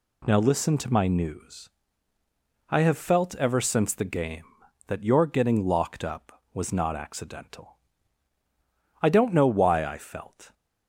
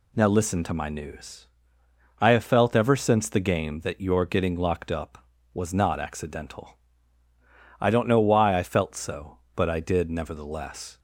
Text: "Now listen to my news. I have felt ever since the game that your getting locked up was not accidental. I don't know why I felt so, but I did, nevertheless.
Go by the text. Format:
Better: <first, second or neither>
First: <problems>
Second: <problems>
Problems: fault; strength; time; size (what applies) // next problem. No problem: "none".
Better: second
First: stops before "so but I did nevertheless"; at 10.5 s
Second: none